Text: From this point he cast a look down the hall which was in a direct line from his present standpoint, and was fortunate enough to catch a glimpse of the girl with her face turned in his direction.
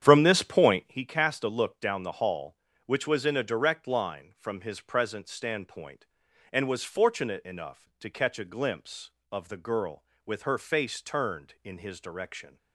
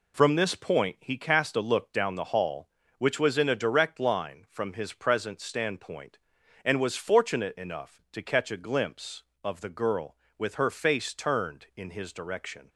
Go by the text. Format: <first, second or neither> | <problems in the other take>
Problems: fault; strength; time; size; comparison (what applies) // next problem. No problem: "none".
second | starts louder than the rest; strong; until 0.9 s; 9.5 dB